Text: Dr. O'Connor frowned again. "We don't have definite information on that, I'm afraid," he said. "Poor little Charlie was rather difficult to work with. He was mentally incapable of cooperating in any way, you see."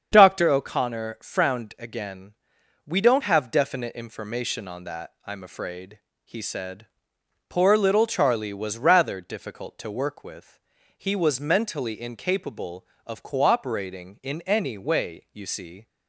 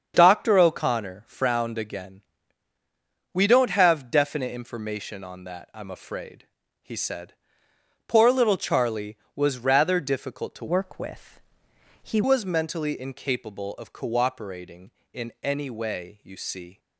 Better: first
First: starts louder than the rest; strong; until 1.1 s; 7.5 dB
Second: starts louder than the rest; strong; until 1.1 s; 7.5 dB // changes voice from "work" to "He"; from 10.6 to 12.2 s; 1.6 s long

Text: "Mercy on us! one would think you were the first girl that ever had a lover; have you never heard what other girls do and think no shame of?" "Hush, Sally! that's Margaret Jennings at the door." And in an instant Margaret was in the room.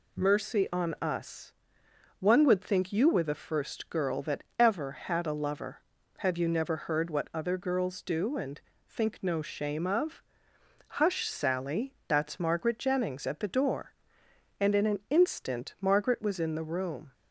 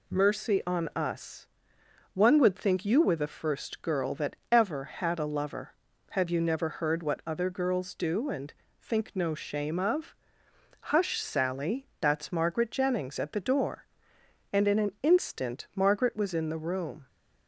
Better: neither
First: pauses between "that" and "ever"; slight; at 4.4 s; 0.16 s long // pauses between "and" and "think"; slight; at 8.6 s; 0.26 s long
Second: pauses between "that" and "ever"; slight; at 4.3 s; 0.16 s long // pauses between "and" and "think"; slight; at 8.5 s; 0.26 s long

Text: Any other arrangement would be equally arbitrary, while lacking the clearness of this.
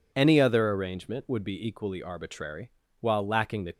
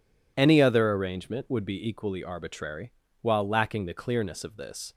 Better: second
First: stops before "clearness of this"; at 3.7 s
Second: none

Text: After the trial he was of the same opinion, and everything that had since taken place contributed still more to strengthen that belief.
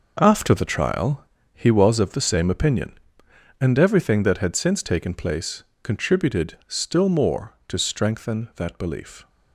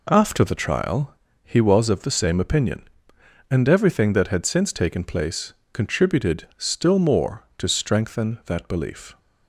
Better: second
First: gets quieter; strong; throughout; 9.5 dB // pauses between "trial" and "he"; slight; at 1.2 s; 0.30 s long // pauses between "place" and "contributed"; slight; at 5.6 s; 0.22 s long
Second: pauses between "trial" and "he"; slight; at 1.1 s; 0.30 s long // pauses between "place" and "contributed"; slight; at 5.5 s; 0.22 s long

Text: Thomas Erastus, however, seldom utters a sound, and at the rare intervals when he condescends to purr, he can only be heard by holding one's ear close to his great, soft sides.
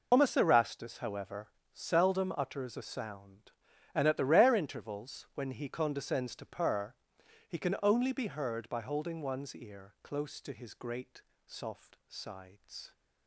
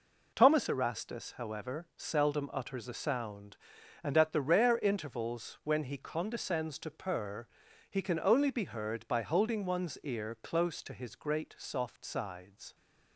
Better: second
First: loses the start of "Thomas"; at 0.1 s; 95 ms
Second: none

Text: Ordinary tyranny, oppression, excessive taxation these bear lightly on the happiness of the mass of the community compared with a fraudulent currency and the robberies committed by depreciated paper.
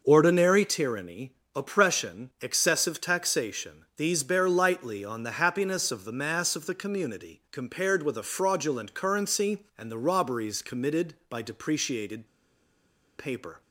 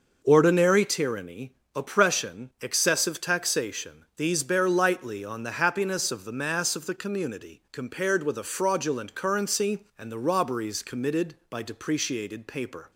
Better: second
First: pauses between "depreciated" and "paper"; noticeable; at 12.2 s; 0.91 s long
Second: none

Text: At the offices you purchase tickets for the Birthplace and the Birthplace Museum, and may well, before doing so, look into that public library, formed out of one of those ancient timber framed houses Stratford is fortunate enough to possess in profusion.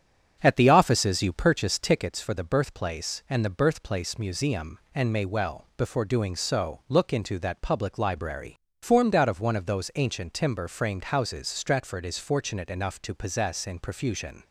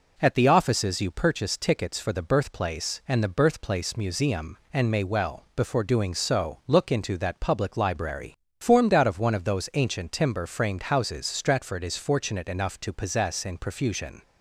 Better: second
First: starts louder than the rest; strong; until 2.2 s; 8 dB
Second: none

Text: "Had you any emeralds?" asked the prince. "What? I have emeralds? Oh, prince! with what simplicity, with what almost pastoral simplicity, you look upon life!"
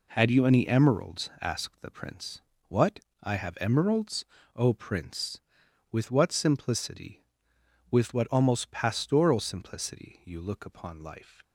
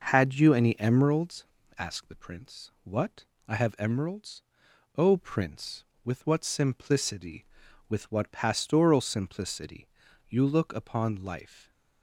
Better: first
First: none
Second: skips "almost"; at 8.2 s

